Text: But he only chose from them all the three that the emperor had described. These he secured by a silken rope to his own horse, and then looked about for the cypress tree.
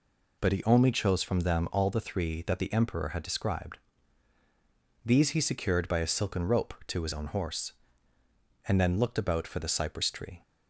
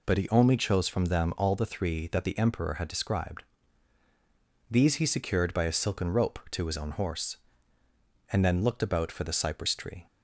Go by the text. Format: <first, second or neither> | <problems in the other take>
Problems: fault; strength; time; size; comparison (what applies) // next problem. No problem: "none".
neither | none